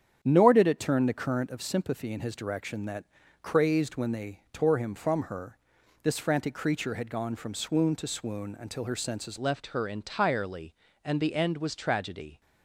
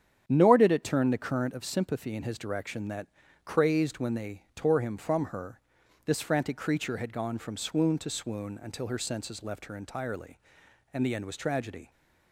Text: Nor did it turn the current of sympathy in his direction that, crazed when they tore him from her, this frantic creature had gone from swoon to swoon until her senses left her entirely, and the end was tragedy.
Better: second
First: starts louder than the rest; strong; until 1.2 s; 8.5 dB // changes voice at "left"; from 9.3 s on; 3.1 s long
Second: starts louder than the rest; strong; until 1.2 s; 8.5 dB

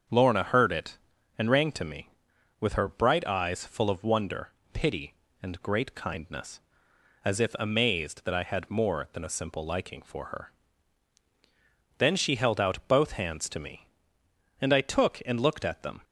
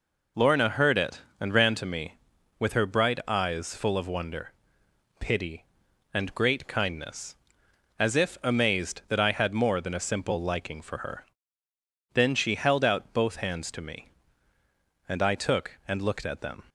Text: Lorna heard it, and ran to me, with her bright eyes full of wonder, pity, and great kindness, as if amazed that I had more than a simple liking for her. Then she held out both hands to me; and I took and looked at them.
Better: second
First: starts louder than the rest; until 1.5 s; 7 dB // says "rang" for "ran"; at 1.4 s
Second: none

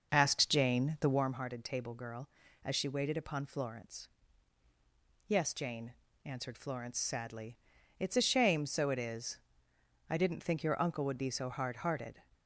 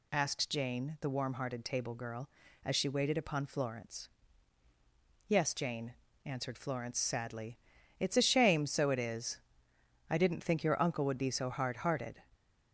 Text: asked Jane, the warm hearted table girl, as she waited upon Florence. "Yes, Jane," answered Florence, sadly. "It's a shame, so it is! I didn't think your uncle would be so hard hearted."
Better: second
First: starts louder than the rest; noticeable; until 1.4 s; 6 dB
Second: none

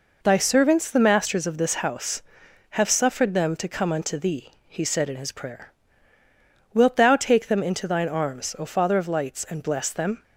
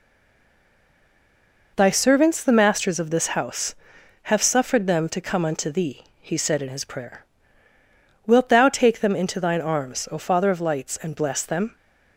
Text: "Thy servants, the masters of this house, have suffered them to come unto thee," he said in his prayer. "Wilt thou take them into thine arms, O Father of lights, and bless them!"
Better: first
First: none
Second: stays silent before the first word; noticeable; until 1.7 s; 1.7 s long

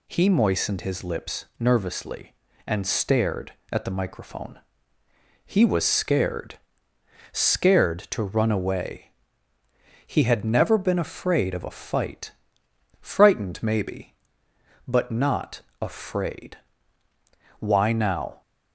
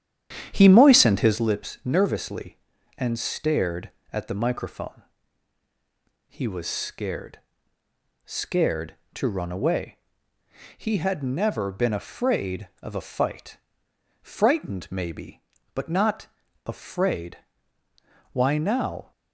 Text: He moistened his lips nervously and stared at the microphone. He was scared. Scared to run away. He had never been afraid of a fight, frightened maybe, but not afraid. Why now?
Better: first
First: pauses between "not" and "afraid"; slight; at 15.6 s; 0.20 s long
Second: starts louder than the rest; strong; until 1.5 s; 9.5 dB // pauses between "not" and "afraid"; at 16.2 s; 0.38 s long

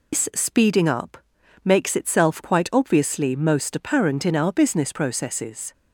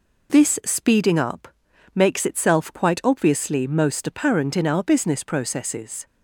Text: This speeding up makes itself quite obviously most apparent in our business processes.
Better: second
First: loses the start of "This"; at 0.1 s; 130 ms // pauses between "up" and "makes"; at 1.1 s; 0.44 s long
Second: pauses between "up" and "makes"; at 1.4 s; 0.44 s long

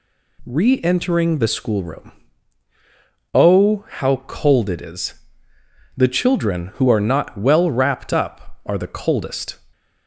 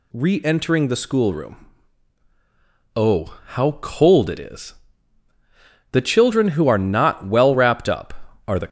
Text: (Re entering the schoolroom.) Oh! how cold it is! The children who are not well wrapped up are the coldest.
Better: first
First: none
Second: stops before "coldest"; at 8.6 s

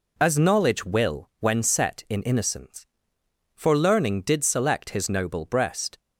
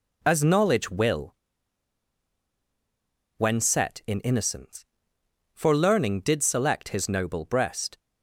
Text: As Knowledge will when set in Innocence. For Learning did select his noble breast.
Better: first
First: none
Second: pauses between "will" and "when"; strong; at 1.3 s; 2.0 s long

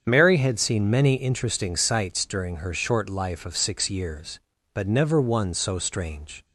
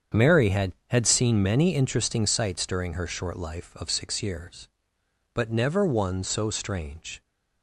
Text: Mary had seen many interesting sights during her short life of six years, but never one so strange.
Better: first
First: starts louder than the rest; strong; until 1.0 s; 7.5 dB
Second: starts louder than the rest; strong; until 1.3 s; 7.5 dB // says "had" twice; at 0.8 s

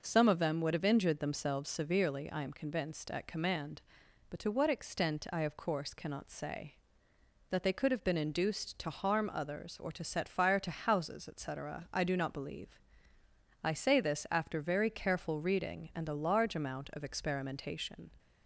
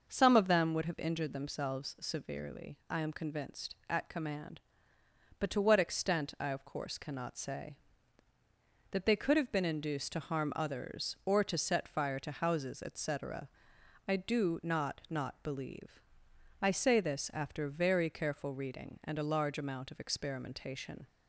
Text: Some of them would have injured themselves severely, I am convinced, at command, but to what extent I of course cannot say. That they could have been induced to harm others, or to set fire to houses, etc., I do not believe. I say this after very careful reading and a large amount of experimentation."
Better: first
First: none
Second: starts louder than the rest; noticeable; until 1.0 s; 6 dB // says "not" twice; at 15.0 s

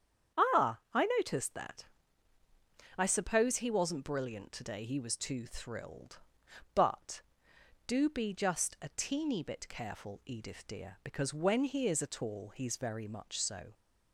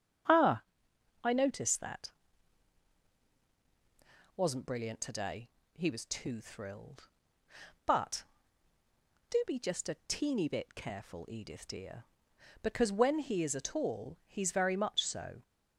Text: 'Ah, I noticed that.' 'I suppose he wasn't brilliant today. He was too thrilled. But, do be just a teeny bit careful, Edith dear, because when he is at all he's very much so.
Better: first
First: starts louder than the rest; strong; until 1.5 s; 8 dB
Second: starts louder than the rest; strong; until 1.8 s; 7.5 dB // skips "I suppose he"; at 3.2 s

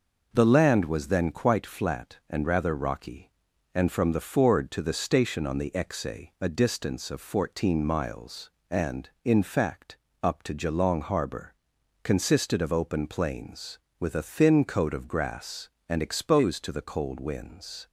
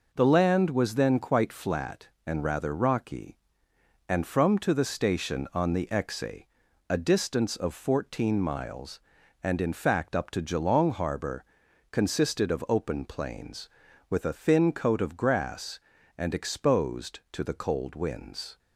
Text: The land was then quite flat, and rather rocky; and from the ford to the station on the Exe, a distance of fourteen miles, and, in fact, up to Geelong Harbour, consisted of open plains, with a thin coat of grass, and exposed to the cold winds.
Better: first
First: none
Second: skips "the ford"; at 4.5 s

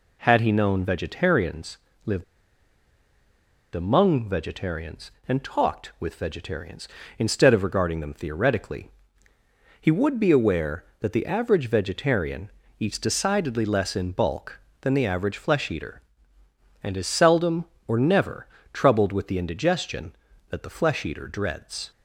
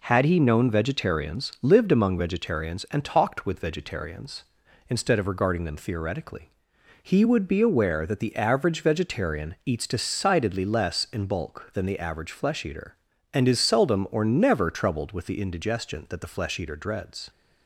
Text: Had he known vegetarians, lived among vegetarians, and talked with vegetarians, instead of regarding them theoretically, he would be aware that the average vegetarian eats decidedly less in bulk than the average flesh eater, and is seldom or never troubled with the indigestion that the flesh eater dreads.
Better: second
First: pauses between "lived" and "among"; strong; at 2.2 s; 1.5 s long // pauses between "vegetarian" and "eats"; slight; at 12.4 s; 0.30 s long // pauses between "never" and "troubled"; slight; at 18.4 s; 0.26 s long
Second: none

